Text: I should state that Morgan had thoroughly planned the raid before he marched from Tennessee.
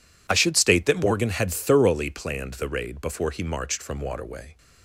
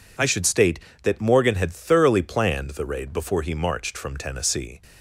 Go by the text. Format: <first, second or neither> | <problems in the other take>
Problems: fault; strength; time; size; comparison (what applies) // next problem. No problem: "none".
second | says "Waterway" for "Tennessee"; at 4.0 s